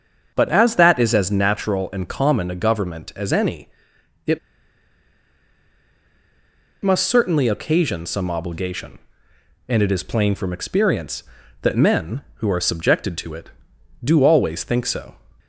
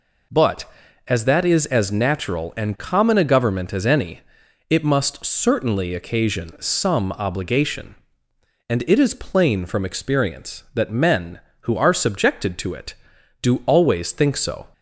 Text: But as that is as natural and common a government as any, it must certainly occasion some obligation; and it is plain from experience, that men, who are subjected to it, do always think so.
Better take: second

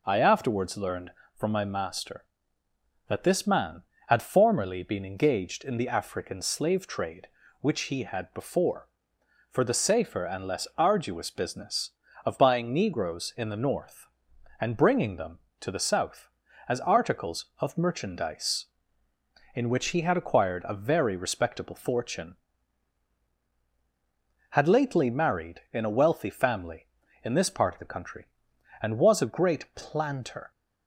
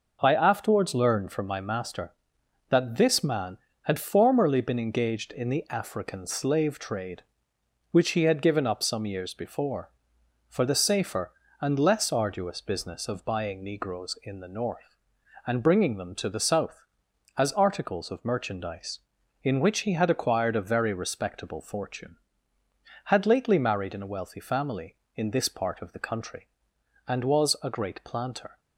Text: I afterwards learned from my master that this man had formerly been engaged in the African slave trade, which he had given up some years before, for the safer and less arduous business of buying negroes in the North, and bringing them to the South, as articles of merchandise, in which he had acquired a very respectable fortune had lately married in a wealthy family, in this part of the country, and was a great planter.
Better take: second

